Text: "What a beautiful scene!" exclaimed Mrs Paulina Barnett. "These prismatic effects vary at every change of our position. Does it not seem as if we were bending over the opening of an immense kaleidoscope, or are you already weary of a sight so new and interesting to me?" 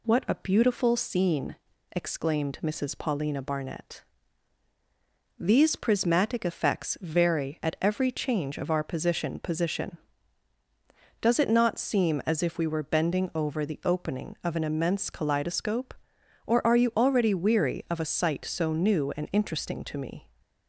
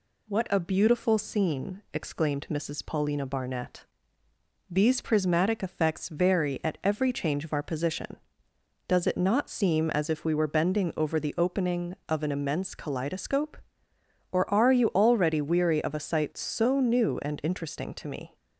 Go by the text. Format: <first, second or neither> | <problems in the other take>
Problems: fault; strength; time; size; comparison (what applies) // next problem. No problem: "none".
second | says "position" twice; at 9.3 s